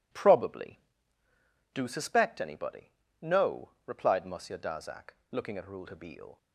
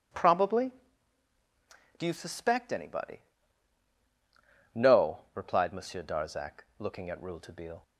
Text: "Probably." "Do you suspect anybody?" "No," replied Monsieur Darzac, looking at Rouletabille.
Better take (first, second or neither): second